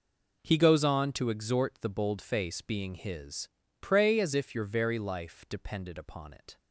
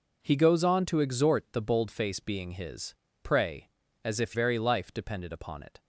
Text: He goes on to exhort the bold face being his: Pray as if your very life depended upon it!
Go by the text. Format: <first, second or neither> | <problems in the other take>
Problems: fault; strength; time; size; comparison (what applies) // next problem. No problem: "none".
first | skips "your"; at 4.3 s